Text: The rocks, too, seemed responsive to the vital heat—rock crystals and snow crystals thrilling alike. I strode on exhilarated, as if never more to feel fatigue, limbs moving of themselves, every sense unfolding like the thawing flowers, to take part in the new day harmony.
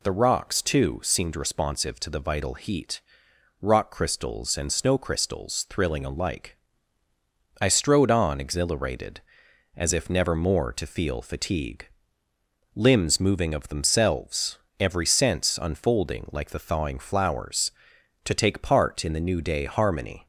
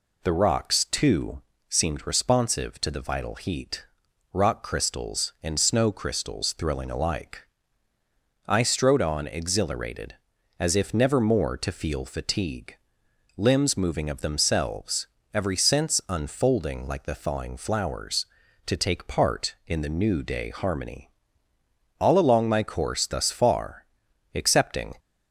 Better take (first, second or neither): first